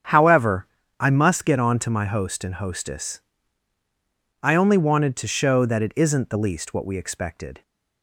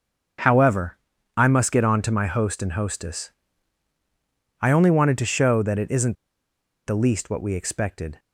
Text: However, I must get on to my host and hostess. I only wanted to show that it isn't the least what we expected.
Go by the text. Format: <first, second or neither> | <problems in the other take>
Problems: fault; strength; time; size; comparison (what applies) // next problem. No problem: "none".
first | starts louder than the rest; strong; until 1.8 s; 7 dB; strong in the first // pauses between "isn't" and "the"; noticeable; at 6.1 s; 0.71 s long